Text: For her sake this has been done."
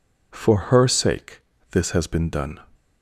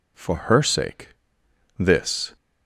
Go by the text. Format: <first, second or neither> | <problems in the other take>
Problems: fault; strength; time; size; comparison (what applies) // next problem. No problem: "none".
first | pauses between "sake" and "this"; noticeable; at 1.0 s; 0.68 s long; slight in the first // stops before "has been done"; at 2.3 s